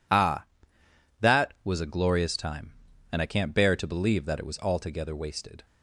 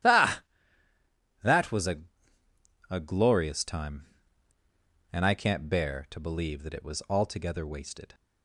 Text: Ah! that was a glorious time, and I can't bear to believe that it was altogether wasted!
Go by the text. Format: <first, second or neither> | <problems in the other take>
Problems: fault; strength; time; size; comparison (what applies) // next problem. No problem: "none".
first | starts louder than the rest; strong; until 2.9 s; 13 dB // says "a" twice; at 2.9 s